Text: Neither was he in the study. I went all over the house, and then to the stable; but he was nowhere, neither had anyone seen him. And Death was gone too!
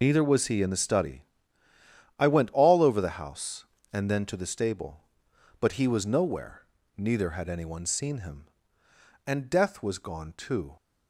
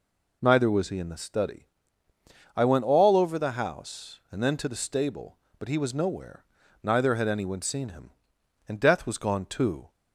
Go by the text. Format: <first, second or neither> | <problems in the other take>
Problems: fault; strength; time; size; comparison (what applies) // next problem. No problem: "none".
second | loses the start of "Neither"; at 0.0 s; 70 ms